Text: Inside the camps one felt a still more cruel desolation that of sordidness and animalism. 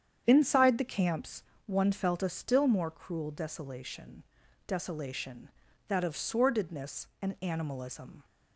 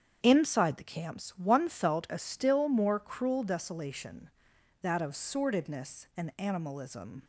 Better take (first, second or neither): second